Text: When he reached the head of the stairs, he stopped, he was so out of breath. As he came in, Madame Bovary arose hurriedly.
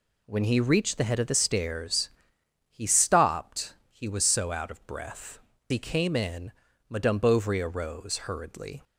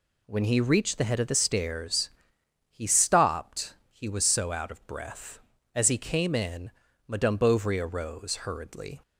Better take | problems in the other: second | skips "As"; at 5.5 s

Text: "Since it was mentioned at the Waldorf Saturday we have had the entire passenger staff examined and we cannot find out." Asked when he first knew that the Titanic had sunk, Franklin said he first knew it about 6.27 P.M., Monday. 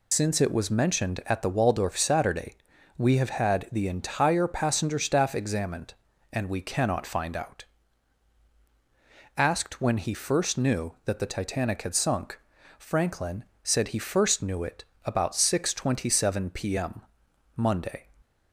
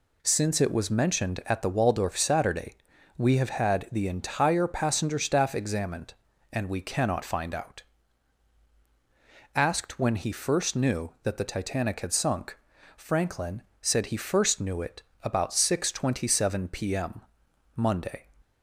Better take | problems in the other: second | loses the start of "Since"; at 0.1 s; 95 ms // pauses between "Saturday" and "we"; at 2.5 s; 0.40 s long; also in the second // pauses between "Franklin" and "said"; slight; at 13.4 s; 0.18 s long; slight in the second // pauses between "it" and "about"; slight; at 14.8 s; 0.18 s long; slight in the second

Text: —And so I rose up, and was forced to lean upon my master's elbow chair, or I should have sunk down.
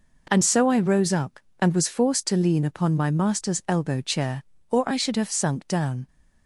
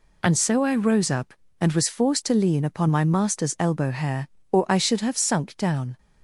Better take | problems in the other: first | says "hair" for "chair"; at 3.9 s

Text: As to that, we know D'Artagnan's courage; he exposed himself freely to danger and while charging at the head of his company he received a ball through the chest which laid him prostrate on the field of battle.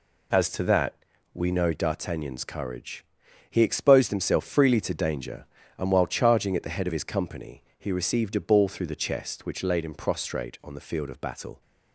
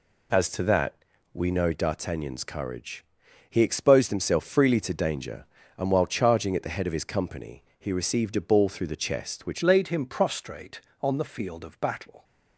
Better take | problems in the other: first | changes voice at "laid"; from 9.6 s on; 2.6 s long

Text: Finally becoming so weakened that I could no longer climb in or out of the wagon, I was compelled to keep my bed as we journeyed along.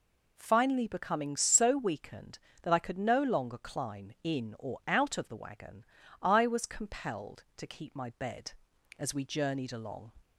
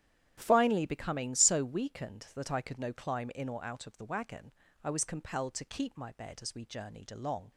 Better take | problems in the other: first | starts louder than the rest; strong; until 1.3 s; 10 dB // skips "longer"; at 2.9 s

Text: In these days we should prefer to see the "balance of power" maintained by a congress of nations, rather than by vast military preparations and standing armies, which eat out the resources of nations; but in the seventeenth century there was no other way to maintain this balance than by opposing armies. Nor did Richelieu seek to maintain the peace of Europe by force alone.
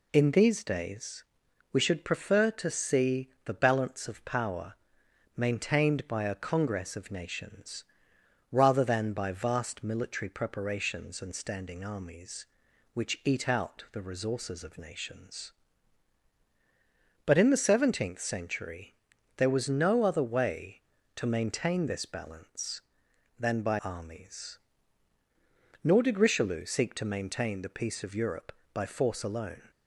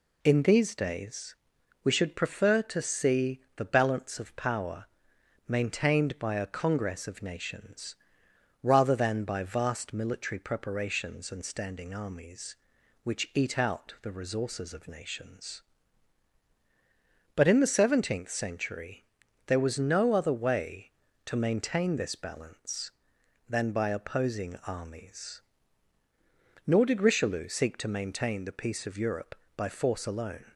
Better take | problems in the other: second | pauses between "days" and "we"; noticeable; at 1.2 s; 0.48 s long; noticeable in the second // pauses between "see" and "the"; slight; at 3.2 s; 0.16 s long; slight in the second // pauses between "power" and "maintained"; noticeable; at 4.7 s; 0.64 s long; noticeable in the second // pauses between "century" and "there"; at 18.9 s; 0.42 s long; also in the second // skips "opposing"; at 23.8 s

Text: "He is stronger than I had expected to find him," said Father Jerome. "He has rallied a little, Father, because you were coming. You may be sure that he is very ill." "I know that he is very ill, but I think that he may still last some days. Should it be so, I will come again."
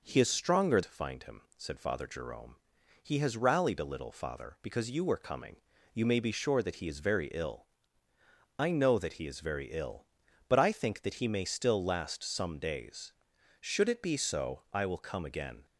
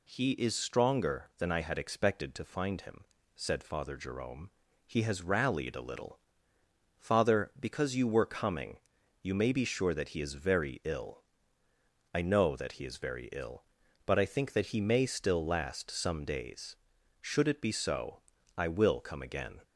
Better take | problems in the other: second | skips "than I had expected"; at 0.8 s

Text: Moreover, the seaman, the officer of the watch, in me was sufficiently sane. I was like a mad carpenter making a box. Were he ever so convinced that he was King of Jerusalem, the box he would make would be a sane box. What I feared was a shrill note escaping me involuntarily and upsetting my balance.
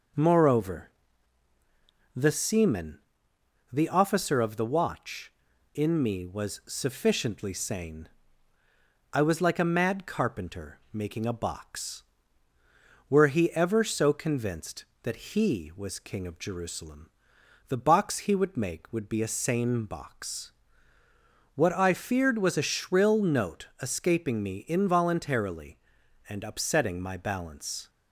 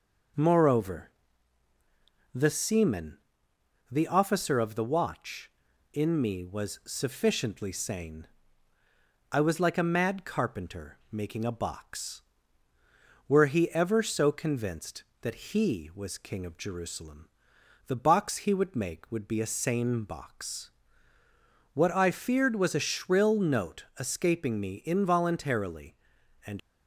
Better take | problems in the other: first | stops before "upsetting my balance"; at 26.5 s

